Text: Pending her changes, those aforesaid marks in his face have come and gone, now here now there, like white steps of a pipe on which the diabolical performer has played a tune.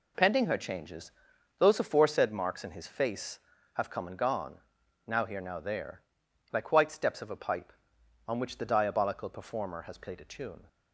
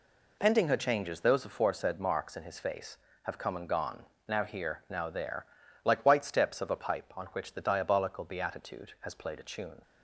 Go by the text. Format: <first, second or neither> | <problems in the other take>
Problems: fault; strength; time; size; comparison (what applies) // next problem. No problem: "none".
first | says "beatitude" for "performer"; at 8.2 s